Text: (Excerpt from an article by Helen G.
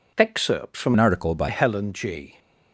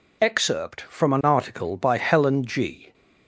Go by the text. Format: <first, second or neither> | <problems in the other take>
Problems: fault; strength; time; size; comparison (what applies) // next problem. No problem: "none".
second | changes voice from "an" to "by"; from 0.9 to 1.4 s; 0.5 s long